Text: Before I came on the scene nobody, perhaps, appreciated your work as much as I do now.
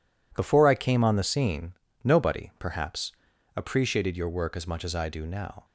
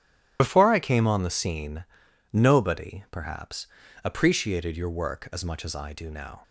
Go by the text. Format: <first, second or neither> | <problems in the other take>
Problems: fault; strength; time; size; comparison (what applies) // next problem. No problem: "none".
first | loses the start of "Before"; at 0.3 s; 75 ms // starts louder than the rest; strong; until 1.4 s; 12 dB // pauses between "scene" and "nobody"; noticeable; at 1.8 s; 0.50 s long; slight in the first